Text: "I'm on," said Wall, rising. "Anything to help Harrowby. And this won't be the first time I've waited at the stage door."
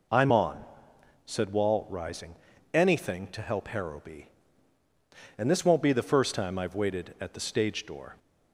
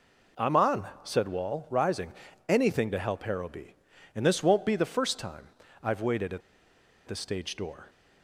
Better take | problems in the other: first | pauses between "time" and "I've"; slight; at 5.4 s; 0.36 s long // pauses between "at" and "the"; noticeable; at 6.4 s; 0.66 s long

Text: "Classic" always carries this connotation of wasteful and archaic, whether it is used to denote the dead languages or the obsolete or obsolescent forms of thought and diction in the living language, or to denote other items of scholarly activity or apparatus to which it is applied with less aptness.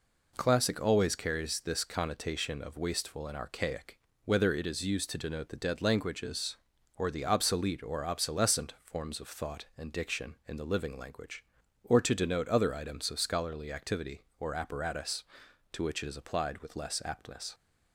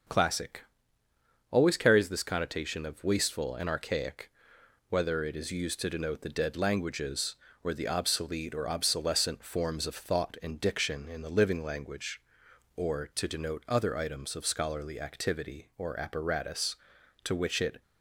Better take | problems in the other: first | starts louder than the rest; until 1.9 s; 6.5 dB // pauses between "Classic" and "always"; noticeable; at 0.6 s; 0.86 s long // stops before "is applied with less aptness"; at 17.8 s

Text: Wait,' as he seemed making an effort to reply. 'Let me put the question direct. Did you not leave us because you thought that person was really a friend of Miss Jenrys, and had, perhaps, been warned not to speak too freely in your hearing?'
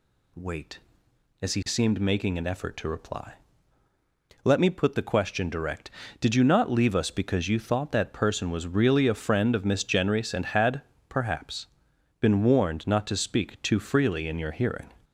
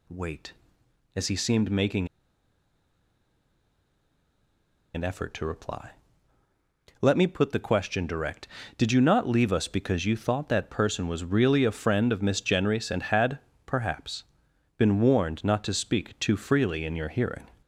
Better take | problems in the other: first | pauses between "making" and "an"; strong; at 2.0 s; 2.8 s long

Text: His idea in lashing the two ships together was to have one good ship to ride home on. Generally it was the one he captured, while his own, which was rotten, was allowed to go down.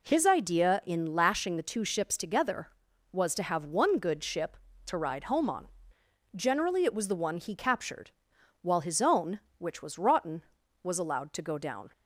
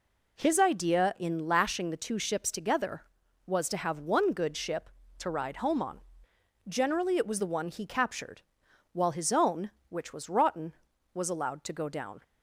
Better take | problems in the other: neither | none

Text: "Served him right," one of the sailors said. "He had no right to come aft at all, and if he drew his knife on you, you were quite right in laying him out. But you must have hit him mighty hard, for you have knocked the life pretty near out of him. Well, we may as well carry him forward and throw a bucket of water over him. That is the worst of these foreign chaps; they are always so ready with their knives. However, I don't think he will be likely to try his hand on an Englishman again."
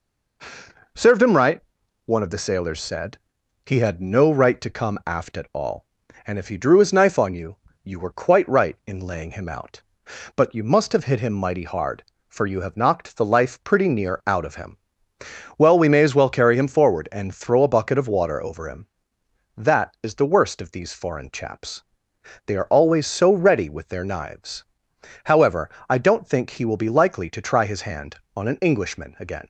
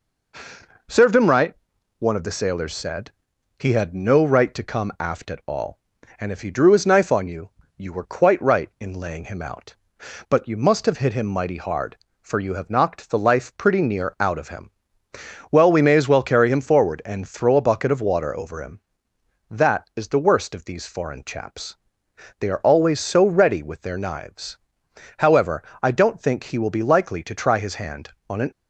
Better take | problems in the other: first | stops before "Englishman again"; at 28.5 s

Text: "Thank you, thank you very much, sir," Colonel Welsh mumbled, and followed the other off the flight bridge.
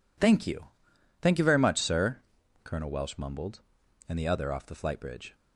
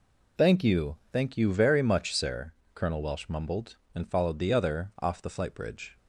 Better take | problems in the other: second | skips "followed"; at 4.1 s

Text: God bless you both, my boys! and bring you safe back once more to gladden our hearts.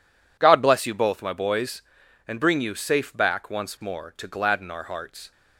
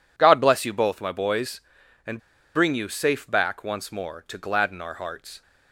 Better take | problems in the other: first | pauses between "and" and "bring"; at 2.1 s; 0.36 s long

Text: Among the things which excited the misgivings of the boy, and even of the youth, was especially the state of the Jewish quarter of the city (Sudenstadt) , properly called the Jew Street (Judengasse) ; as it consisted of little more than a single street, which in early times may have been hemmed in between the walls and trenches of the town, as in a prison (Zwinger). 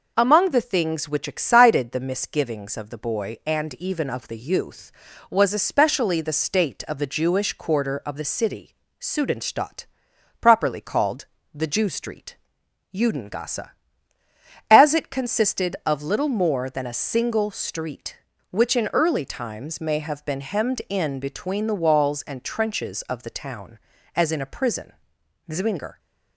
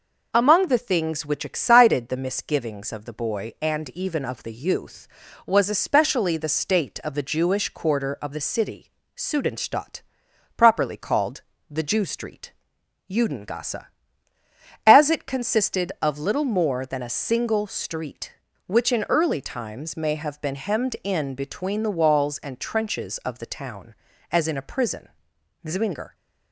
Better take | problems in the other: neither | pauses between "called" and "the"; slight; the same in both

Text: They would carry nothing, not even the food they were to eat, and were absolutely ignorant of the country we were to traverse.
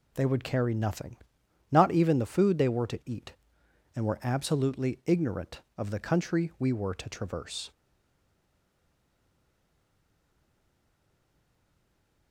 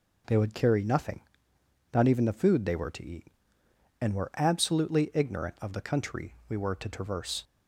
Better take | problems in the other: second | stays silent after the last word; strong; from 7.7 s on; 4.6 s long

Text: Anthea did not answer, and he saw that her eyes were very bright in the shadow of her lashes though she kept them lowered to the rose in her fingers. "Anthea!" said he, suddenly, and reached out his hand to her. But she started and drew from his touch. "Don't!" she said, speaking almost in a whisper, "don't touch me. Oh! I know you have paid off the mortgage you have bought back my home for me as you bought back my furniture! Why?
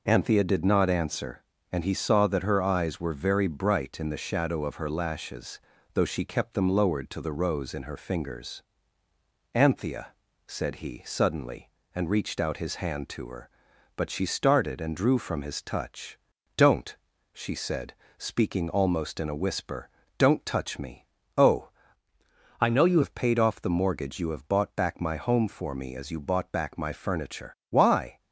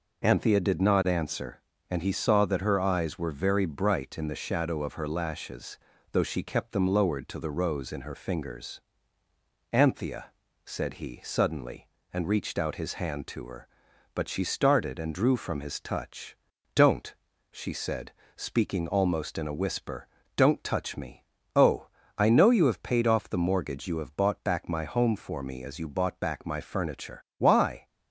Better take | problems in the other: second | pauses between "lashes" and "though"; slight; at 5.5 s; 0.36 s long; slight in the second // changes voice from "I" to "you"; from 22.6 to 23.0 s; 0.4 s long

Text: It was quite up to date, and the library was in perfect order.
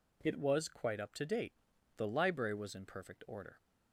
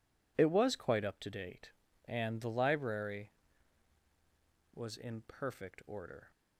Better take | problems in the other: second | skips "and"; at 1.7 s

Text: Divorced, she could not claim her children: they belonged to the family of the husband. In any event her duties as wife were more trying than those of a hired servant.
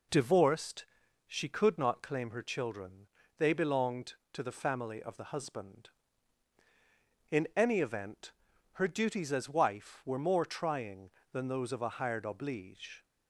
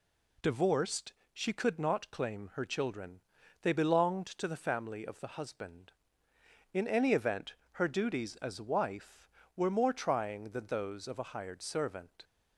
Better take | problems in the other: second | pauses between "event" and "her"; at 8.3 s; 0.40 s long; slight in the second // says "oblige" for "servant"; at 12.2 s

